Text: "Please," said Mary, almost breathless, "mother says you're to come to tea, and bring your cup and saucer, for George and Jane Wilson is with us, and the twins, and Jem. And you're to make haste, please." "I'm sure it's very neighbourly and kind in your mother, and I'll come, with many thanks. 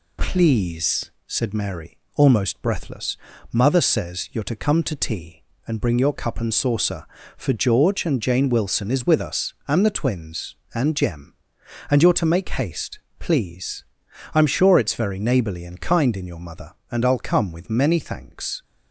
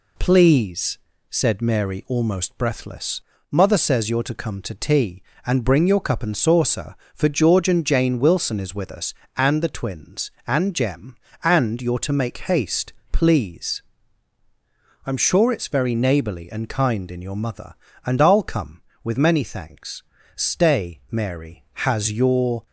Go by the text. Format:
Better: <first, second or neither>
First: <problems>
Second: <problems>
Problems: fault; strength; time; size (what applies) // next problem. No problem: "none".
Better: first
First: none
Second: goes on to say "Stay Mary has your"; strong; from 20.3 s on; 2.3 s long